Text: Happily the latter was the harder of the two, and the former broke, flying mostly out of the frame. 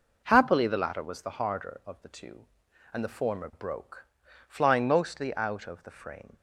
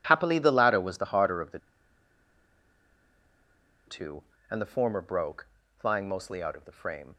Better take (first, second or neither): first